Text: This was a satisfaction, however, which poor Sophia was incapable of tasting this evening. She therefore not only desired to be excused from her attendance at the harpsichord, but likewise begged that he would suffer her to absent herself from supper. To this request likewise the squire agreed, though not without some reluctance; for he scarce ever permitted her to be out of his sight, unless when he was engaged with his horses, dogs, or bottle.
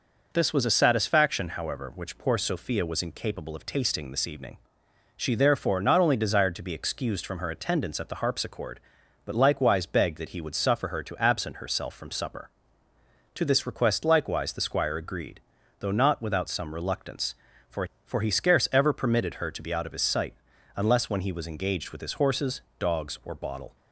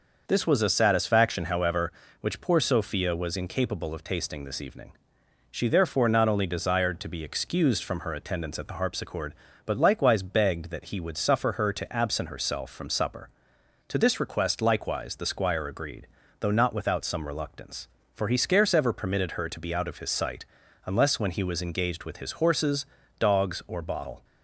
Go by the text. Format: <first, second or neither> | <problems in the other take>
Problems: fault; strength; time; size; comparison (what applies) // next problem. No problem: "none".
second | says "for" twice; at 18.0 s